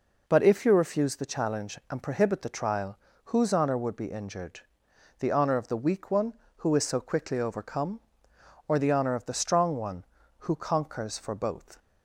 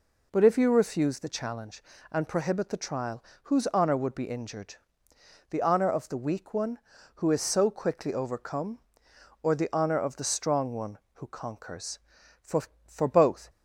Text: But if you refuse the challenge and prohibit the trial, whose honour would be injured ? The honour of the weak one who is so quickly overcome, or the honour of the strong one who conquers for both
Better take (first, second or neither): first